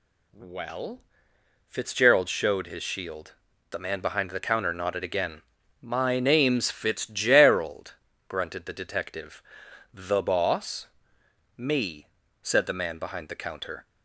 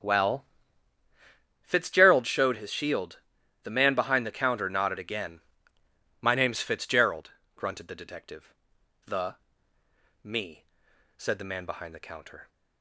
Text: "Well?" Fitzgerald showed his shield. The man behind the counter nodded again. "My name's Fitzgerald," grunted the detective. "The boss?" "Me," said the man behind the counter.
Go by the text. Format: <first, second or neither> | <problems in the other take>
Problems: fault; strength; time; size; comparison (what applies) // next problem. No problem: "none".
first | starts louder than the rest; strong; until 2.1 s; 8.5 dB // skips "boss"; at 9.7 s